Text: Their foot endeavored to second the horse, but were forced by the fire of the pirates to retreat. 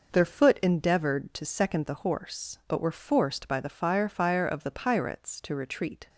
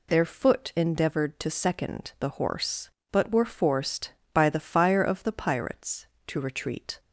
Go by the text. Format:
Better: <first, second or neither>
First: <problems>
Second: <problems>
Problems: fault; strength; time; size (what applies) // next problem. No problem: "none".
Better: second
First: says "fire" twice; at 4.0 s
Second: none